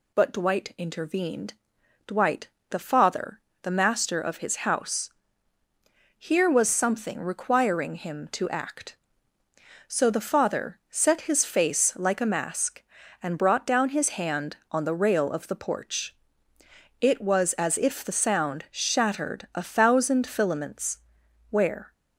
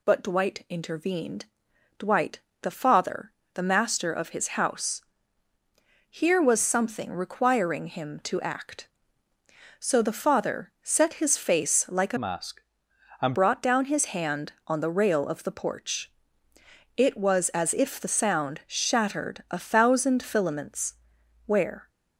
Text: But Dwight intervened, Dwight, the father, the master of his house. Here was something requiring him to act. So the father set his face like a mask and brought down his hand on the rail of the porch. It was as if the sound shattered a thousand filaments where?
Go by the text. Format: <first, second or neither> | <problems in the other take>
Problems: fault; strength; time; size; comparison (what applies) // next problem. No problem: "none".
first | changes voice from "mask" to "and"; from 12.1 to 13.3 s; 1.2 s long // pauses between "filaments" and "where"; noticeable; at 20.9 s; 0.52 s long; noticeable in the first